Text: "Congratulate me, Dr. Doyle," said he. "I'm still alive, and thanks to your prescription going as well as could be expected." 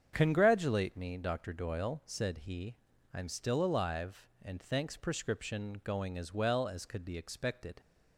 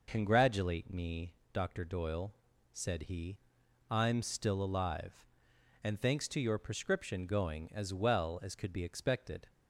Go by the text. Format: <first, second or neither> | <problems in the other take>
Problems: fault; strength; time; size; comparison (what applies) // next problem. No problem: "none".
second | starts louder than the rest; strong; until 1.1 s; 7.5 dB // skips "to your"; at 4.9 s